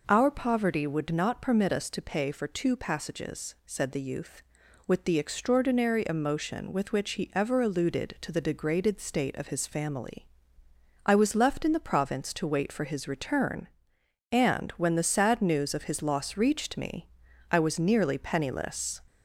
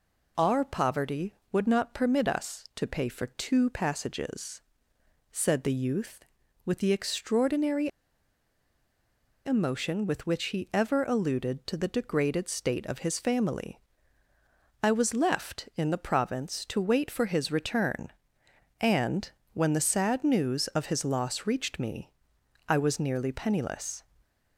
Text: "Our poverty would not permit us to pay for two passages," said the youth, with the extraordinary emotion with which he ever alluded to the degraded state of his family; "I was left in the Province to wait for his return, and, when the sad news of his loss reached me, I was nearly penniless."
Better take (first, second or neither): first